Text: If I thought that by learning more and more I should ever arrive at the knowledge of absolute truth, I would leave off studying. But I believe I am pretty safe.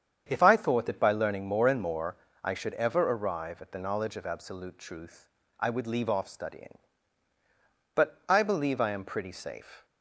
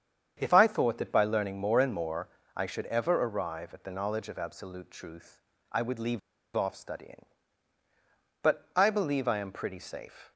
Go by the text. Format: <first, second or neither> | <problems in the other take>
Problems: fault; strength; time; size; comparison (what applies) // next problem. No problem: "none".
first | starts louder than the rest; strong; until 1.4 s; 8 dB; strong in the first // pauses between "more" and "I"; slight; at 2.2 s; 0.28 s long; slight in the first // pauses between "leave" and "off"; at 6.1 s; 0.36 s long